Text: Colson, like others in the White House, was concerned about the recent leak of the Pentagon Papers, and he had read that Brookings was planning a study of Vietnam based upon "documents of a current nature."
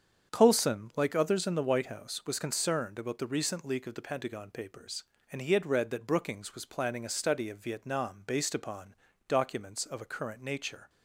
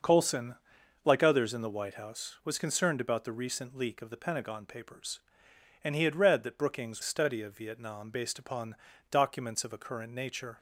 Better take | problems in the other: first | starts louder than the rest; until 1.5 s; 6.5 dB; strong in the first // skips "was planning a"; at 7.0 s // pauses between "upon" and "documents"; slight; at 8.7 s; 0.34 s long; slight in the first

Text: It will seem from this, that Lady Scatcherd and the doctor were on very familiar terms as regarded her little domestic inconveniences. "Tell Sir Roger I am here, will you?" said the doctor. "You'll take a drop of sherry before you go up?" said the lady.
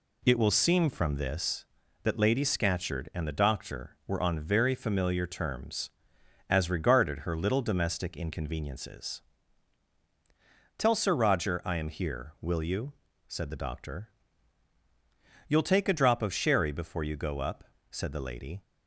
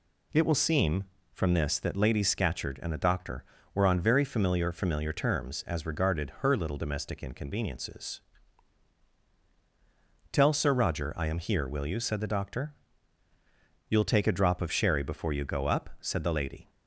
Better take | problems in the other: first | says "familiar" twice; at 4.7 s

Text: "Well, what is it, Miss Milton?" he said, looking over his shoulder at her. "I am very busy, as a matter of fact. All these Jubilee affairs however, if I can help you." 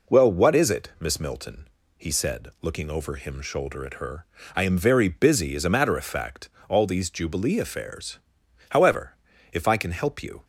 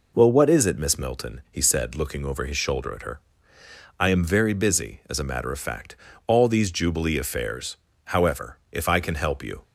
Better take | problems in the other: second | says "him" for "his"; at 3.1 s // pauses between "affairs" and "however"; noticeable; at 8.2 s; 0.48 s long; slight in the second

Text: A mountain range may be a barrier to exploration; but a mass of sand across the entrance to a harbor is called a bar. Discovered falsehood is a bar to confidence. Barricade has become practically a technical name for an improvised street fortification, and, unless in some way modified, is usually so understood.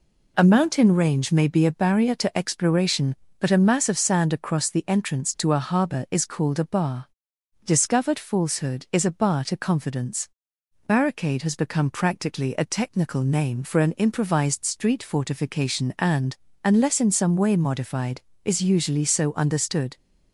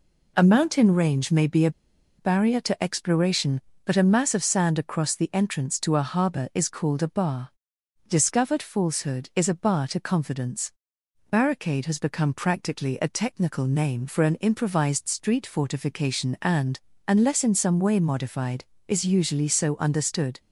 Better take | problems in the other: first | pauses between "a" and "barrier"; noticeable; at 1.6 s; 0.49 s long

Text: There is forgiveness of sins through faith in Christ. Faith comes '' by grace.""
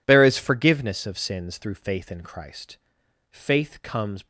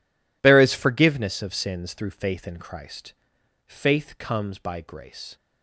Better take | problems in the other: second | stops before "by grace"; at 4.2 s

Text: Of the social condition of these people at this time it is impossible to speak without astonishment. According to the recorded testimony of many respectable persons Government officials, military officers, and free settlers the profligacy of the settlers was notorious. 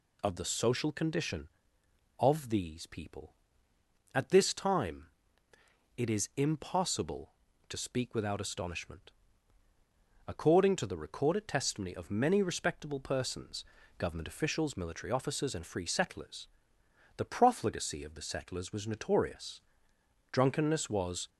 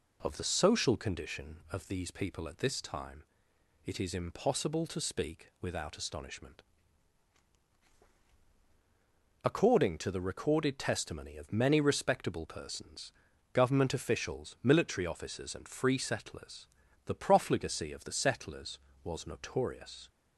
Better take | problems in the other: second | pauses between "time" and "it"; noticeable; at 5.0 s; 0.92 s long; noticeable in the second // pauses between "persons" and "Government"; slight; at 13.6 s; 0.34 s long; also in the second // pauses between "settlers" and "the"; noticeable; at 16.4 s; 0.68 s long; also in the second // goes on to say "Drunkenness was"; noticeable; from 20.3 s on; 0.96 s long

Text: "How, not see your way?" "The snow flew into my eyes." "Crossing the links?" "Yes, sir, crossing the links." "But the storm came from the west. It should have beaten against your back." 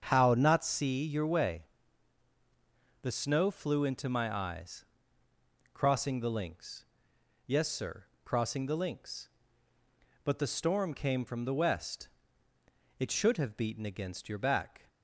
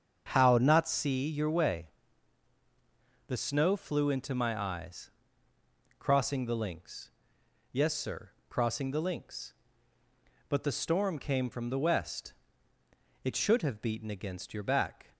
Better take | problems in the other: neither | starts louder than the rest; strong; the same in both

